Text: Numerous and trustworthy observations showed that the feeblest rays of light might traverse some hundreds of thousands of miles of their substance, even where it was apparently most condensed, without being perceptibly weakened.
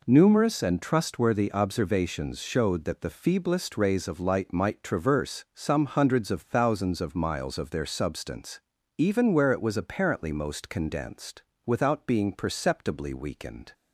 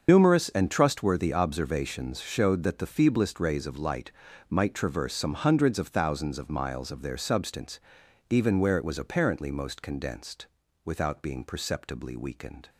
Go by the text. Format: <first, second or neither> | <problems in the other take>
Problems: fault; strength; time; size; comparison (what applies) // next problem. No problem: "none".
first | loses the start of "Numerous"; at 0.0 s; 100 ms // starts louder than the rest; until 1.0 s; 7 dB // pauses between "light" and "might"; slight; at 4.1 s; 0.36 s long